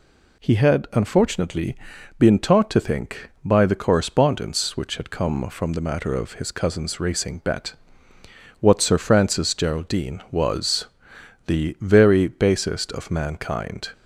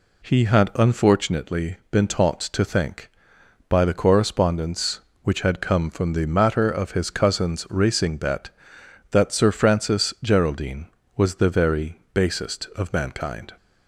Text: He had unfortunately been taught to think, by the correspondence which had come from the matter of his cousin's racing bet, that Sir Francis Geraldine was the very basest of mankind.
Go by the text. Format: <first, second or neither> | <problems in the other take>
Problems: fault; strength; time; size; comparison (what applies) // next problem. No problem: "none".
second | pauses between "unfortunately" and "been"; at 1.7 s; 0.42 s long; slight in the second // says "what" for "that"; at 8.6 s // pauses between "was" and "the"; noticeable; at 10.8 s; 0.62 s long